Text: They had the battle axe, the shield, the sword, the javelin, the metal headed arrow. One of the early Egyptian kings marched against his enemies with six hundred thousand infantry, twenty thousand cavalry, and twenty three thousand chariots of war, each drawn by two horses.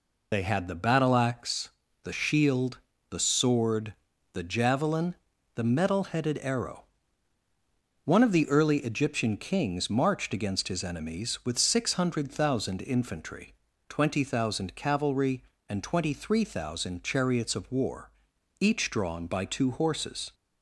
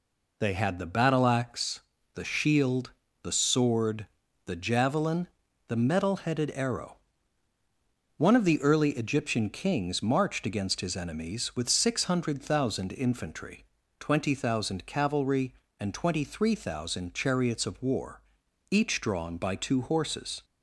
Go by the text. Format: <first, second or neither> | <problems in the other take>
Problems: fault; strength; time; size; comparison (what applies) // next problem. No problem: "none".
second | loses the start of "They"; at 0.3 s; 30 ms